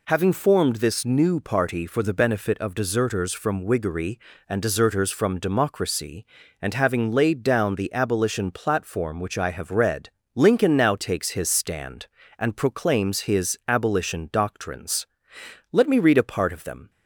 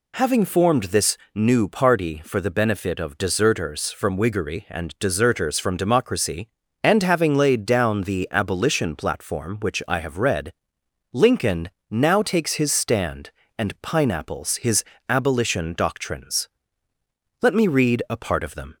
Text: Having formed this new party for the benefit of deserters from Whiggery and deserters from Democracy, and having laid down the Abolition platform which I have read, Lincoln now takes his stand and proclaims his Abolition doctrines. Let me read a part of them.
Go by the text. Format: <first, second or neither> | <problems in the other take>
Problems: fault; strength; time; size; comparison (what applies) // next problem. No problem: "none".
first | pauses between "this" and "new"; slight; at 1.1 s; 0.18 s long // pauses between "Lincoln" and "now"; slight; at 11.6 s; 0.22 s long // says "pineapples" for "proclaims"; at 13.8 s // pauses between "his" and "Abolition"; slight; at 14.8 s; 0.24 s long